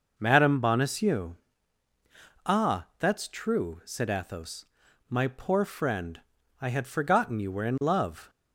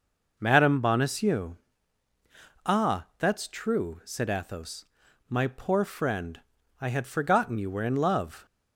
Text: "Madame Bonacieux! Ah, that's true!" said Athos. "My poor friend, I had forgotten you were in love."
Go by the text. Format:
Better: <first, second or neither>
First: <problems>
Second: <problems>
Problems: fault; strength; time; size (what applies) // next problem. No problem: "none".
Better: neither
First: none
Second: none